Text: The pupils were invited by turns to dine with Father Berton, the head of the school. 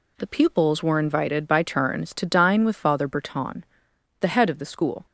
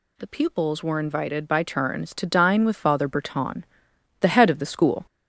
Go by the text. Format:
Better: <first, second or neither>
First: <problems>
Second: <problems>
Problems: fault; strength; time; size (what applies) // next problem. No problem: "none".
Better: first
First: none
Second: gets louder; noticeable; throughout; 4.5 dB